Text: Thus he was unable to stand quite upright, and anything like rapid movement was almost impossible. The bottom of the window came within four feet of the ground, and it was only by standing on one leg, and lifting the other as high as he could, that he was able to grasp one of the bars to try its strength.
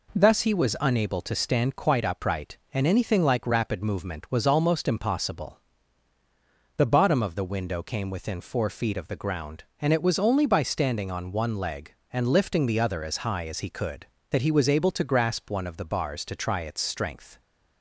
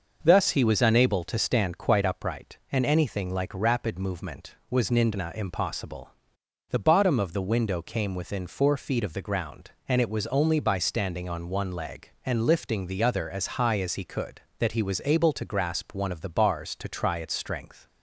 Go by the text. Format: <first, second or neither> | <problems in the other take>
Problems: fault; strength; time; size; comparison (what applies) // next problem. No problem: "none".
first | starts louder than the rest; noticeable; until 1.2 s; 6 dB // says "nindna" for "almost"; at 4.8 s